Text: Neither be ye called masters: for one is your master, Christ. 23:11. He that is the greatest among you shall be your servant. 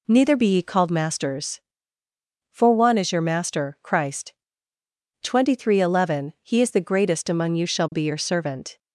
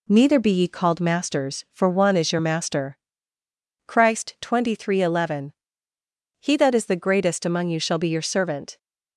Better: second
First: skips "that"; at 6.6 s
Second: none

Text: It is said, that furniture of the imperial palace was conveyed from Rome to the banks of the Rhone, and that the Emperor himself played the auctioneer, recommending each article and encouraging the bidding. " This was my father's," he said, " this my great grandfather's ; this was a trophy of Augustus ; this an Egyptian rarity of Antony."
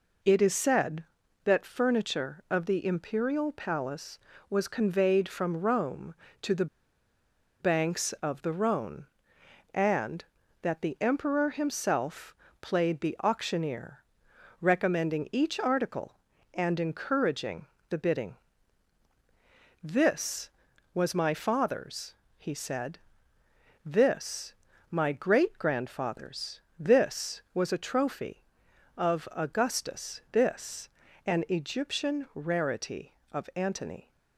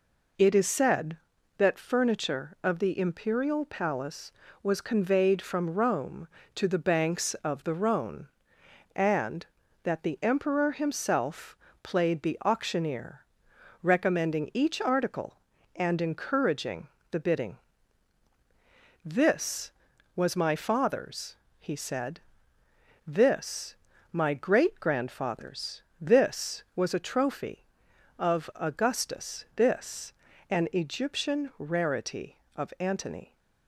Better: second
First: pauses between "the" and "banks"; noticeable; at 6.6 s; 0.94 s long // pauses between "himself" and "played"; slight; at 12.3 s; 0.26 s long // pauses between "encouraging" and "the"; slight; at 17.6 s; 0.22 s long // pauses between "this" and "my"; slight; at 24.5 s; 0.34 s long // pauses between "this" and "an"; slight; at 30.8 s; 0.36 s long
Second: pauses between "himself" and "played"; slight; at 11.5 s; 0.26 s long // pauses between "encouraging" and "the"; slight; at 16.8 s; 0.22 s long // pauses between "this" and "my"; slight; at 23.7 s; 0.34 s long // pauses between "this" and "an"; slight; at 30.1 s; 0.36 s long

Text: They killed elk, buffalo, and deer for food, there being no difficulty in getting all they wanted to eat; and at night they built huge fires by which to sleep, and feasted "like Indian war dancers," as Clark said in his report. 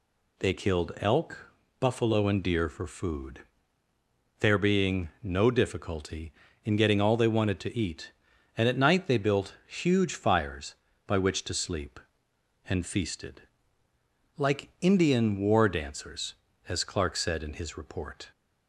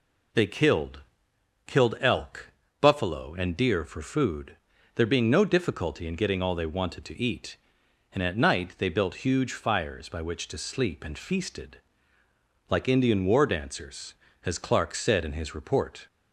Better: first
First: pauses between "feasted" and "like"; noticeable; at 13.4 s; 0.94 s long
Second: says "killed" twice; at 1.6 s // pauses between "feasted" and "like"; noticeable; at 11.8 s; 0.88 s long

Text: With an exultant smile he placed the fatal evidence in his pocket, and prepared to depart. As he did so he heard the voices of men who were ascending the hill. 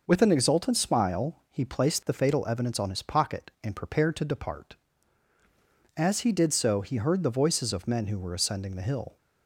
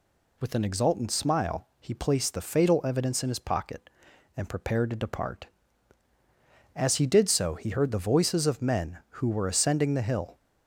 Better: second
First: says "on" for "in"; at 2.7 s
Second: none

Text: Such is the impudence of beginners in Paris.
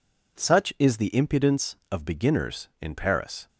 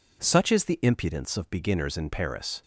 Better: neither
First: none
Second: none

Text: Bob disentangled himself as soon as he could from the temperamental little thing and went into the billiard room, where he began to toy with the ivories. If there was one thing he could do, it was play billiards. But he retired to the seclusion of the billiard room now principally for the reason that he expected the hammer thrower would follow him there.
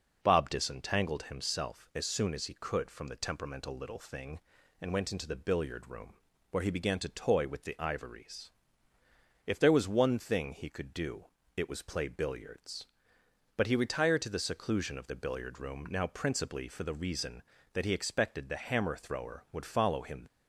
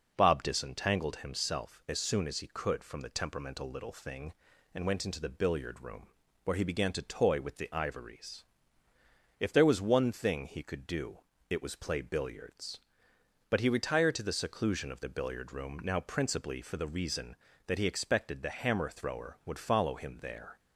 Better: second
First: stops before "there"; at 20.2 s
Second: none

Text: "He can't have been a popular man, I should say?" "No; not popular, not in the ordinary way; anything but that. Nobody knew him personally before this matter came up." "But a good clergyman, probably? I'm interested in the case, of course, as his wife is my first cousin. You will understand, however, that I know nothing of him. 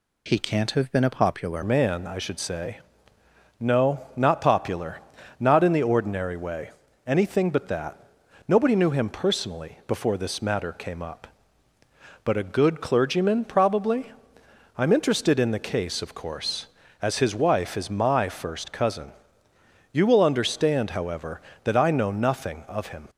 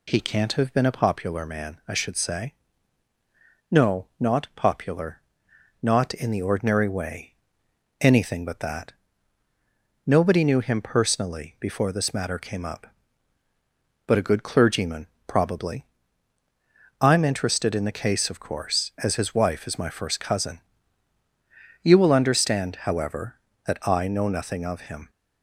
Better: second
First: changes voice at "man"; from 1.6 s on; 21.4 s long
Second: none

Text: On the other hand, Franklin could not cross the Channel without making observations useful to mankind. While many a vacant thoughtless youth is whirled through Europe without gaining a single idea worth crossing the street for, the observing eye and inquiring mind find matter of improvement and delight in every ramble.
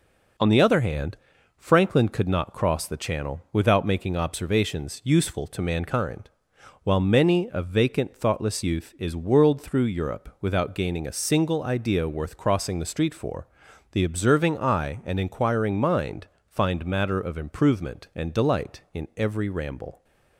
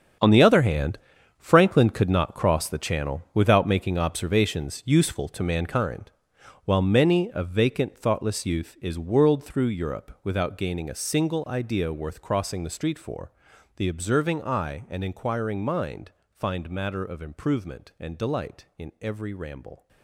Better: first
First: pauses between "mind" and "find"; slight; at 16.2 s; 0.22 s long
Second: gets quieter; strong; throughout; 13 dB // pauses between "mind" and "find"; slight; at 16.1 s; 0.22 s long

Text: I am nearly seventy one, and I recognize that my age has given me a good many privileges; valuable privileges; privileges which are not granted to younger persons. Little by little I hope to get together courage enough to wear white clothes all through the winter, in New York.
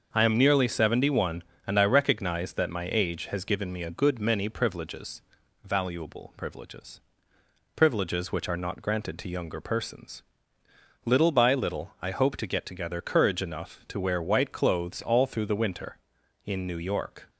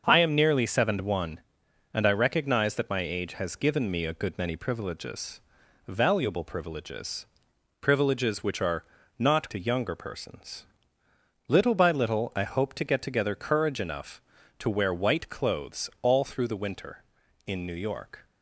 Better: first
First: starts louder than the rest; until 1.1 s; 6.5 dB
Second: starts louder than the rest; until 1.0 s; 6.5 dB // pauses between "are" and "not"; slight; at 8.8 s; 0.32 s long // skips "granted"; at 9.4 s

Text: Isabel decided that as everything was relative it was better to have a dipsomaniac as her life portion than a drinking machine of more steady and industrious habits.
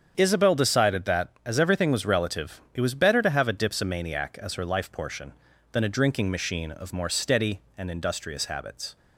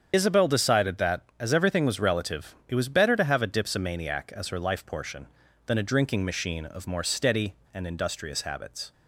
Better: first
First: starts louder than the rest; strong; until 1.1 s; 8 dB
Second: loses the start of "Isabel"; at 0.1 s; 40 ms // starts louder than the rest; strong; until 1.1 s; 7.5 dB

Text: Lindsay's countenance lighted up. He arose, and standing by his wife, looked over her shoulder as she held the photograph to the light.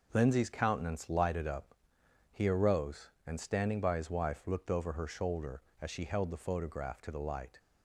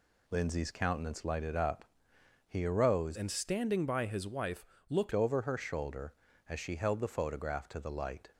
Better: first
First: none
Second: changes voice from "and" to "looked"; from 3.1 to 5.1 s; 2.0 s long

